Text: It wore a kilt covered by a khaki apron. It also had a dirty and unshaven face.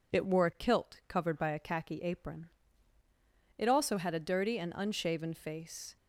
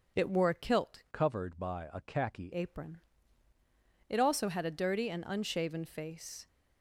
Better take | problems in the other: first | starts louder than the rest; noticeable; until 1.2 s; 6 dB // changes voice from "covered" to "khaki"; from 1.1 to 2.5 s; 1.4 s long

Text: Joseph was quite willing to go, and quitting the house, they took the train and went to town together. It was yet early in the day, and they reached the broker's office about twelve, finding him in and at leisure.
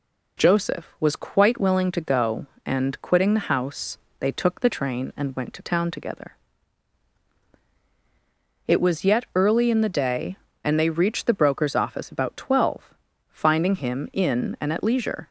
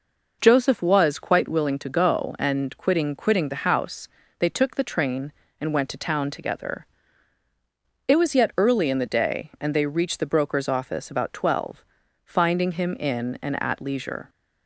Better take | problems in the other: first | says "quitting" twice; at 3.1 s

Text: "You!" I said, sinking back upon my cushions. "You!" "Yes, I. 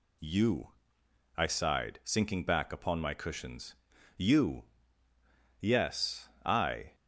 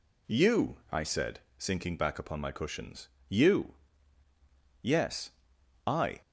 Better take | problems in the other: second | says "sighed" for "said"; at 1.4 s

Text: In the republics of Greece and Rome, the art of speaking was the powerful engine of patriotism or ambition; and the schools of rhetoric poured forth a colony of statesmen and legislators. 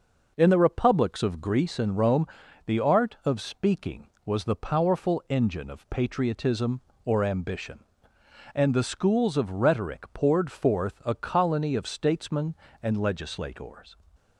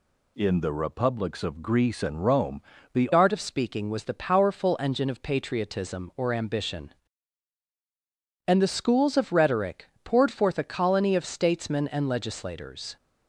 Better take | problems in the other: first | changes voice at "art"; from 3.1 s on; 9.8 s long // pauses between "rhetoric" and "poured"; slight; at 9.8 s; 0.18 s long

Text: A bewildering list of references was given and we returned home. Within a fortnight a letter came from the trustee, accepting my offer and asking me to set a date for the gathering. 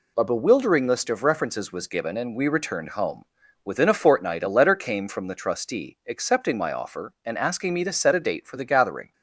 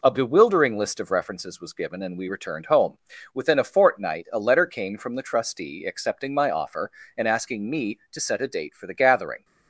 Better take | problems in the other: neither | none

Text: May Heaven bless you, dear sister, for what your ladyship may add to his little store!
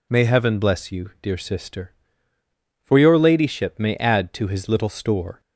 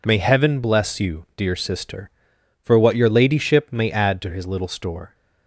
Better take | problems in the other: second | skips "what"; at 2.9 s

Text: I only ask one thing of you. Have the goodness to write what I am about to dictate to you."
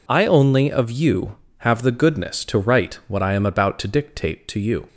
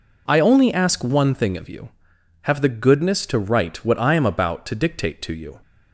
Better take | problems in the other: second | skips "ask one thing"; at 0.7 s

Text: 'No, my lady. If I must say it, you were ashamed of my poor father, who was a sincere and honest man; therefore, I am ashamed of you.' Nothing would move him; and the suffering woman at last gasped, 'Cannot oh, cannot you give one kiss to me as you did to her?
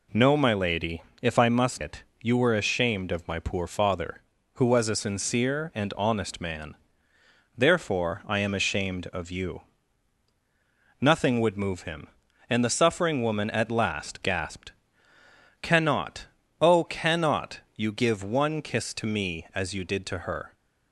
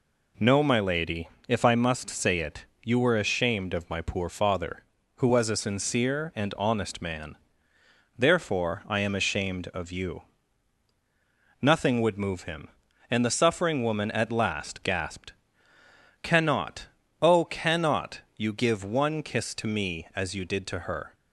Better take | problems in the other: second | skips "say"; at 1.8 s // pauses between "Cannot" and "oh"; slight; at 16.2 s; 0.34 s long; slight in the second

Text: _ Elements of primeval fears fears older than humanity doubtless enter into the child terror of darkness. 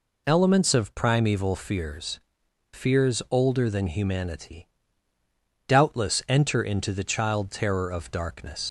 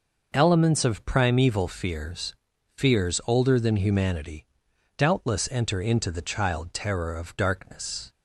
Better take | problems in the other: second | pauses between "fears" and "fears"; noticeable; at 2.1 s; 0.54 s long; also in the second // pauses between "humanity" and "doubtless"; noticeable; at 4.6 s; 0.98 s long; noticeable in the second // leaves "darkness" unfinished; at 8.6 s; 90 ms

